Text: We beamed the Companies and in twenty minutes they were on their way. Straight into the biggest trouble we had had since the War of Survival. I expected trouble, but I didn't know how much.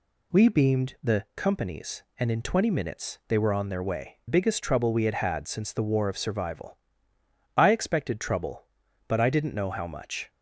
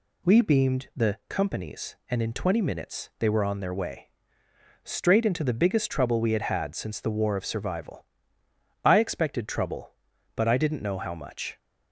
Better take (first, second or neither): second